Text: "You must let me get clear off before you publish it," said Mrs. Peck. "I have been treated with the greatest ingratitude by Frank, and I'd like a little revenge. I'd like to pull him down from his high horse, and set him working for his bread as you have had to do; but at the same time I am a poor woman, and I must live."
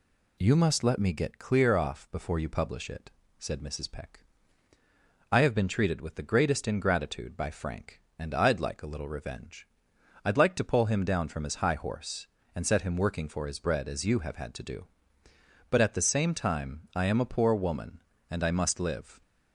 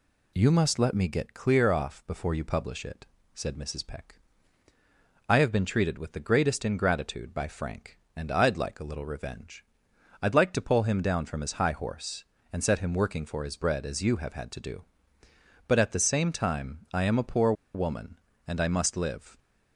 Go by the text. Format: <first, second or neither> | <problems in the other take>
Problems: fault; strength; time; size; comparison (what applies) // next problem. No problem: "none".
first | pauses between "poor" and "woman"; slight; at 17.5 s; 0.21 s long